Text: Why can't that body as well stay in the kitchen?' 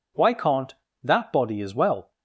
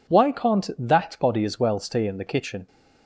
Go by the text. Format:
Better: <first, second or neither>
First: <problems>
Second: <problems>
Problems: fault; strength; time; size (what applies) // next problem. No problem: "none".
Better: second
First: stops before "stay in the kitchen"; at 2.1 s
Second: none